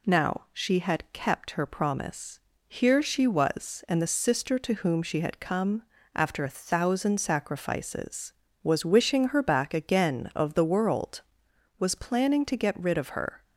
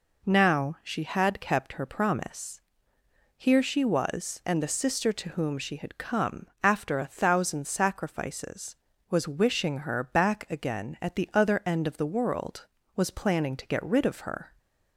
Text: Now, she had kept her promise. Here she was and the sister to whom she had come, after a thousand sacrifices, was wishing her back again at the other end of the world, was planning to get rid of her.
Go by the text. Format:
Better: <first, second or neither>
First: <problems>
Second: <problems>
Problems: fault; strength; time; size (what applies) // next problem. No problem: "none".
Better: second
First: skips "at the other end"; at 10.3 s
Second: none